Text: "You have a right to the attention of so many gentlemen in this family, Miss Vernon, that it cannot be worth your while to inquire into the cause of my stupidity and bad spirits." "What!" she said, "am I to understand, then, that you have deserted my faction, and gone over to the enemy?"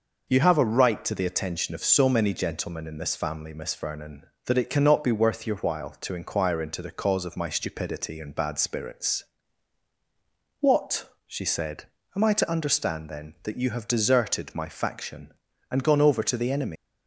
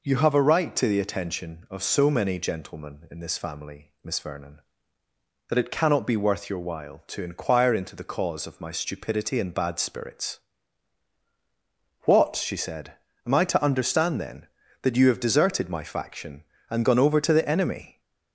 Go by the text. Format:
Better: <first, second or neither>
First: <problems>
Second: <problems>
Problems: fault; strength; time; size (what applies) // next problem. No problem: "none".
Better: second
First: leaves "enemy" unfinished; at 16.7 s; 140 ms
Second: none